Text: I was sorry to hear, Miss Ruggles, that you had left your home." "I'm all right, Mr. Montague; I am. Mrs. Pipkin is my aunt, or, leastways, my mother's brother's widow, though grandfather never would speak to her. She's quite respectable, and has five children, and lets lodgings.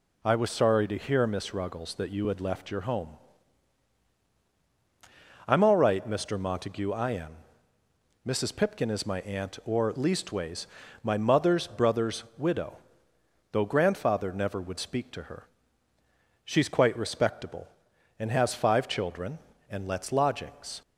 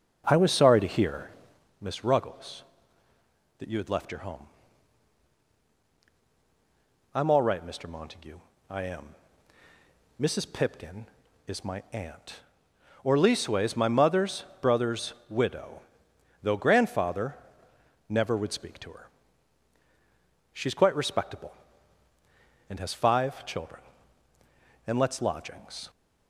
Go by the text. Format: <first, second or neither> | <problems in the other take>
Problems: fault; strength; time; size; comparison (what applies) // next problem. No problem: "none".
first | starts louder than the rest; until 1.6 s; 6.5 dB // pauses between "mother's" and "brother's"; slight; at 14.4 s; 0.18 s long // pauses between "brother's" and "widow"; slight; at 15.1 s; 0.16 s long // pauses between "grandfather" and "never"; noticeable; at 17.3 s; 0.72 s long